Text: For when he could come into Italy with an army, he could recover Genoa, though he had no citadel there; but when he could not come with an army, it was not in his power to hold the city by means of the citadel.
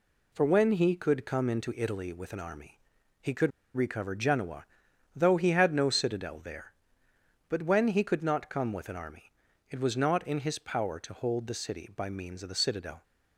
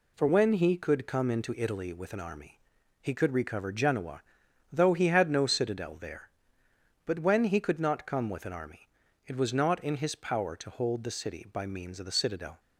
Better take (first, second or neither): second